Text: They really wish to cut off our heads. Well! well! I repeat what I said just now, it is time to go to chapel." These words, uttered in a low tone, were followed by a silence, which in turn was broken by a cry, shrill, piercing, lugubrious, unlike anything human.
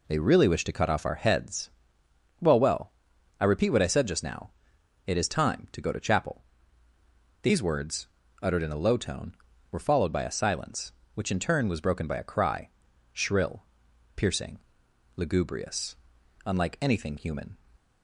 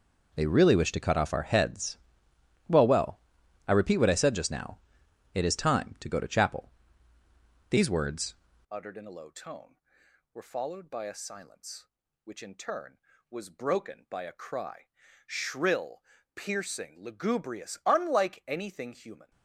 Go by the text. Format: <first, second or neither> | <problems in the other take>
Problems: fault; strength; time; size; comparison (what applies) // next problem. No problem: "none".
first | changes voice at "uttered"; from 8.7 s on; 10.6 s long